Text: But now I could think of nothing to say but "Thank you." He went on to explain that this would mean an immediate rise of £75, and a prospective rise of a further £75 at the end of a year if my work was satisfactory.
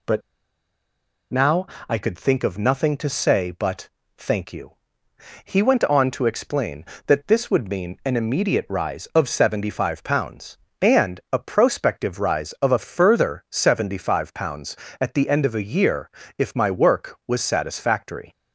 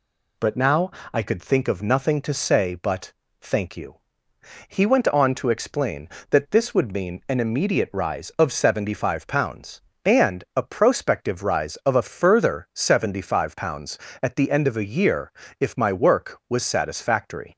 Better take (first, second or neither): second